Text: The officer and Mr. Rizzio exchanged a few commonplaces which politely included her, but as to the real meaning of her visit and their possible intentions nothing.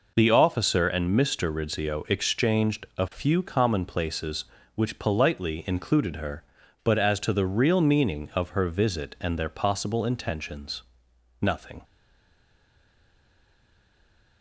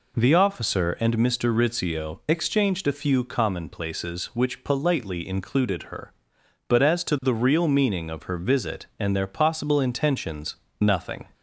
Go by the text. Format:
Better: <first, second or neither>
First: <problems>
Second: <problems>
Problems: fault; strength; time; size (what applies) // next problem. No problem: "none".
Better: second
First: pauses between "intentions" and "nothing"; noticeable; at 10.8 s; 0.62 s long // stays silent after the last word; strong; from 11.8 s on; 2.6 s long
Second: pauses between "intentions" and "nothing"; slight; at 10.5 s; 0.24 s long